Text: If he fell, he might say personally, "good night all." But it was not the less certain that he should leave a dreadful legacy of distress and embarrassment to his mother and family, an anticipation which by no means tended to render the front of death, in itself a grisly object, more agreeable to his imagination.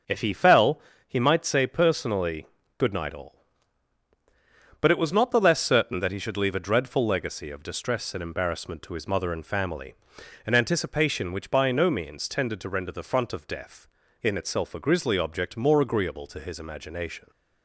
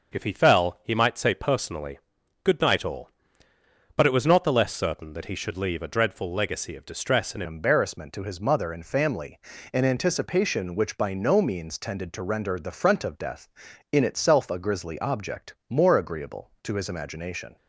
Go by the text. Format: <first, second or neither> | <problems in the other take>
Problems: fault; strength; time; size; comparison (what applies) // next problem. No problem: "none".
first | changes voice at "embarrassment"; from 7.4 s on; 10.1 s long